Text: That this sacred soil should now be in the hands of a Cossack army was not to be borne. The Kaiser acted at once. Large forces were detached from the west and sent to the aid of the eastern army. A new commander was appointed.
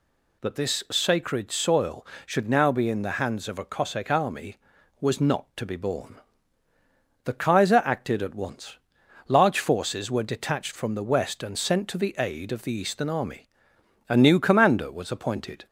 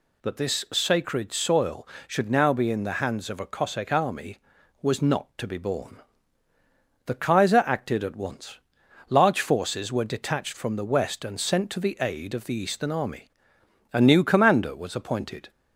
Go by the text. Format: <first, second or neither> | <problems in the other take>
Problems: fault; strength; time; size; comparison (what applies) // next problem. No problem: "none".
neither | none